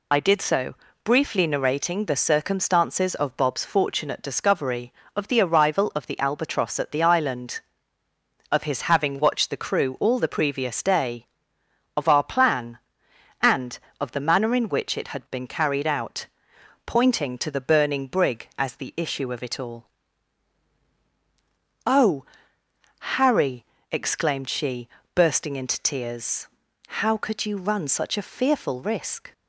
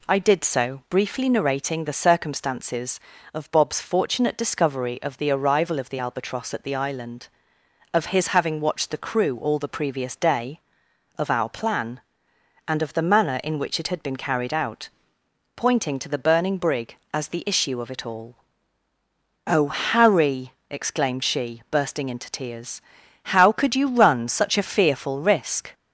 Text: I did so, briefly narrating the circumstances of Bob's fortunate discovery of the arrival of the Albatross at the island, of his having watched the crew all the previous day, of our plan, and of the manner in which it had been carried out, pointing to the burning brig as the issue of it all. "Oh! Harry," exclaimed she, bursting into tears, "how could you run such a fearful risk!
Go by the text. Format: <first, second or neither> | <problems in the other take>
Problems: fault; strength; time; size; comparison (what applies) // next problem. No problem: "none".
second | loses the start of "I"; at 0.1 s; 30 ms